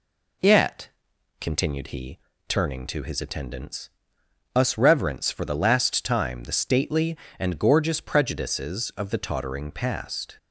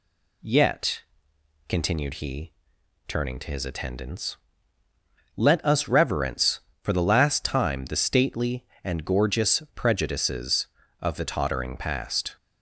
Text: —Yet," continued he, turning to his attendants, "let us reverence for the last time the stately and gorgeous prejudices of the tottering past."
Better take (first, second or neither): second